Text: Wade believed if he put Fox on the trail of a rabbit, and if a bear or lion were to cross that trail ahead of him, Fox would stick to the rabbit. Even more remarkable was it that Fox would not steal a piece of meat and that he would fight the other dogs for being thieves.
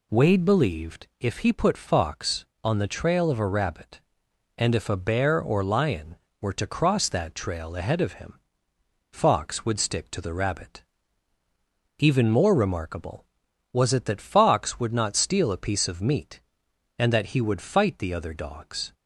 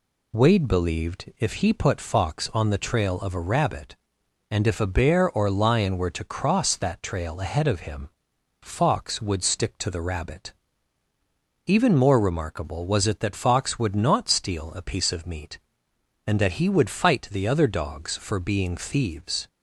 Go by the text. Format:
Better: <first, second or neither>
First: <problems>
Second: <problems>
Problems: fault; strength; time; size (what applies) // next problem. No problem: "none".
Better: second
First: stops before "for being thieves"; at 18.9 s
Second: none